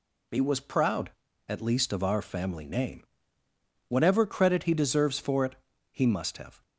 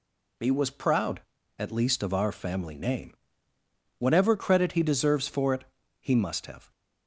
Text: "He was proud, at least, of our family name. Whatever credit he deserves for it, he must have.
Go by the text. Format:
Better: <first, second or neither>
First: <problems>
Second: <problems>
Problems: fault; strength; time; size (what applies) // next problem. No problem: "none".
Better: neither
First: none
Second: none